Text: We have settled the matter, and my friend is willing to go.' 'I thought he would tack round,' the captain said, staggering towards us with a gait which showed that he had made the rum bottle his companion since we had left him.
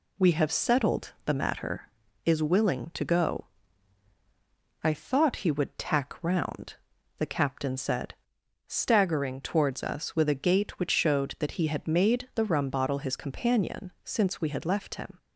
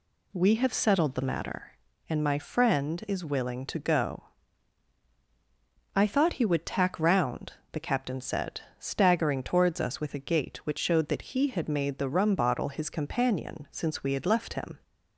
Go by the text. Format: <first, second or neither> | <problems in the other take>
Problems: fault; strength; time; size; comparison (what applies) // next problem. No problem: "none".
second | skips "and my friend"; at 2.0 s